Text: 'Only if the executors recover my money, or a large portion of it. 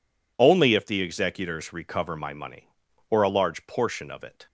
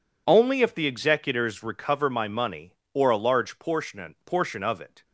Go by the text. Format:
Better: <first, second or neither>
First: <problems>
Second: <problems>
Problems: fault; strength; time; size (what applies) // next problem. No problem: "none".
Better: first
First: none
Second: says "portion" twice; at 4.2 s